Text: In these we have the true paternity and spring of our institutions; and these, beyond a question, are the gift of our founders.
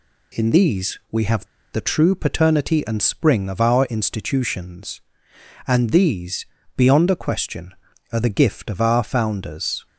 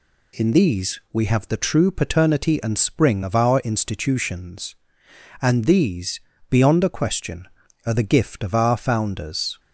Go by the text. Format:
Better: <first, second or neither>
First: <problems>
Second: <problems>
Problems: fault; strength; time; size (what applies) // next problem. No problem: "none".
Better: second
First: pauses between "have" and "the"; slight; at 1.4 s; 0.27 s long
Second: none